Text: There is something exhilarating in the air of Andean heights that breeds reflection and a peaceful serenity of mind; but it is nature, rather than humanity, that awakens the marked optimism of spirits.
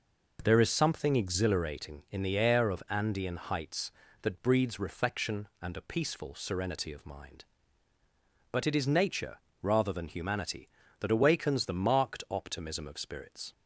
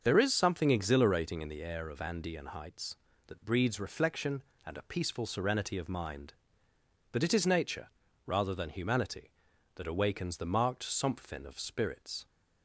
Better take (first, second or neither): first